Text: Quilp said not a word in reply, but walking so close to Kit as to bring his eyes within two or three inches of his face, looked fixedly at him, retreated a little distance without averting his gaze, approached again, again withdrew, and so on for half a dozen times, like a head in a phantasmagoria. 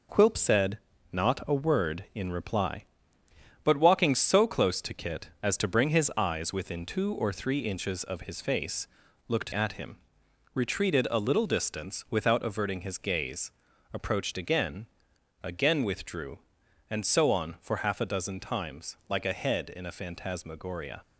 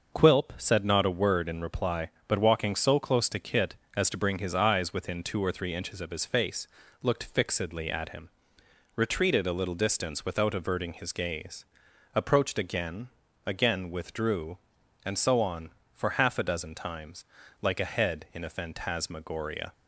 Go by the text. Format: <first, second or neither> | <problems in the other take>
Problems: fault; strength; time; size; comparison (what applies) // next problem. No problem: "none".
second | pauses between "said" and "not"; slight; at 0.7 s; 0.34 s long // skips "fixedly"; at 9.5 s